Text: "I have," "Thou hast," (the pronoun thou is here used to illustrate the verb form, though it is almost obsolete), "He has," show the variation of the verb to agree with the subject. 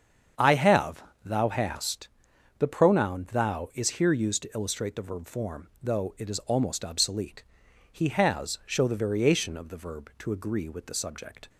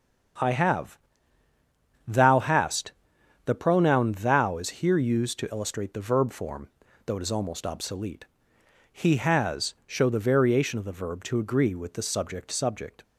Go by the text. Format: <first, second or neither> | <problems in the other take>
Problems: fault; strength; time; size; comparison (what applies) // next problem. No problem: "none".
first | starts louder than the rest; until 2.4 s; 7 dB; strong in the first // says "subject" twice; at 12.5 s